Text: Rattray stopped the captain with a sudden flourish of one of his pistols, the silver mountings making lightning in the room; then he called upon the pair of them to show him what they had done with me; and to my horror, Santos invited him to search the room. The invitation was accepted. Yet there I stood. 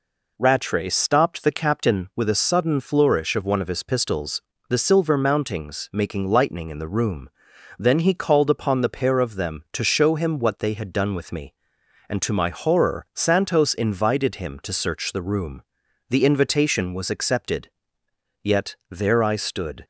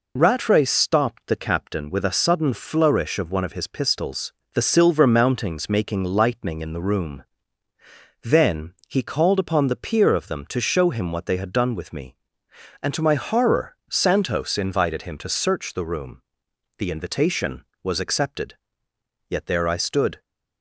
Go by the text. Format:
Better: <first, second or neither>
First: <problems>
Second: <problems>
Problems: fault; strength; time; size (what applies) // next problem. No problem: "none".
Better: first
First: none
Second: pauses between "then" and "he"; slight; at 8.7 s; 0.16 s long // says "peer" for "pair"; at 9.7 s